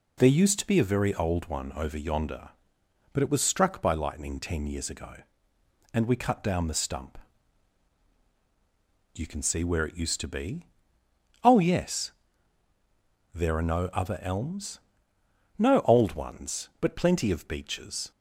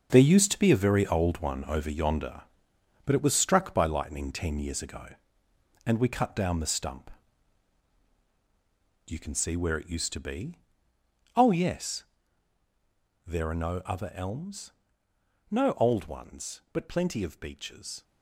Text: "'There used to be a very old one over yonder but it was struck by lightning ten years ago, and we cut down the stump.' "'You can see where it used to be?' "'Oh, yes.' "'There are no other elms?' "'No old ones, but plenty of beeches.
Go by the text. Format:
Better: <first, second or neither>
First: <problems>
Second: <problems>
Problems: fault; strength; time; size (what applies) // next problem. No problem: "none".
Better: first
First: none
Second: gets quieter; strong; throughout; 10 dB